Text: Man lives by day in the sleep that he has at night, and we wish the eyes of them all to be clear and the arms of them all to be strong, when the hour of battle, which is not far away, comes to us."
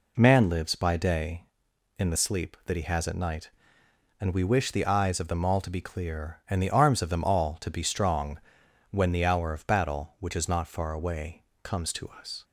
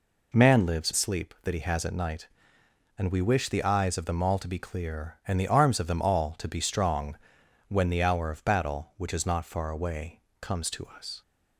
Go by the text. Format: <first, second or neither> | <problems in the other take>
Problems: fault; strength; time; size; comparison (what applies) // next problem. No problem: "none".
first | skips "by day in the"; at 0.9 s